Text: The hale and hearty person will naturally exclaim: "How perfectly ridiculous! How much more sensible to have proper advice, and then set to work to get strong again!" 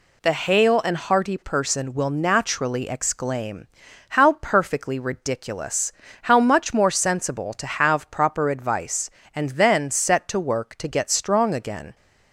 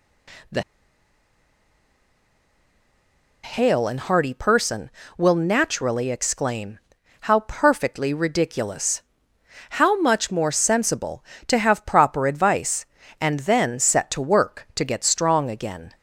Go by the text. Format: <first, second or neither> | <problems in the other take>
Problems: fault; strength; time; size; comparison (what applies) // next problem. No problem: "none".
first | pauses between "The" and "hale"; strong; at 0.6 s; 2.8 s long